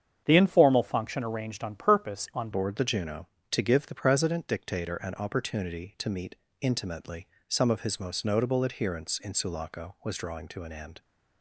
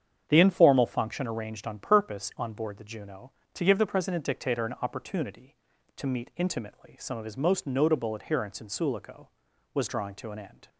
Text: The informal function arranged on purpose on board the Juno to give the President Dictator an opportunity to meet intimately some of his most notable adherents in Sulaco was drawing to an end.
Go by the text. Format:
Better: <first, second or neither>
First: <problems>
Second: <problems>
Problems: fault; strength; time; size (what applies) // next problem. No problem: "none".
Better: second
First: starts louder than the rest; strong; until 1.2 s; 8 dB // changes voice at "board"; from 2.5 s on; 8.4 s long // pauses between "meet" and "intimately"; slight; at 6.3 s; 0.24 s long // pauses between "intimately" and "some"; slight; at 7.2 s; 0.22 s long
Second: starts louder than the rest; strong; until 1.2 s; 8 dB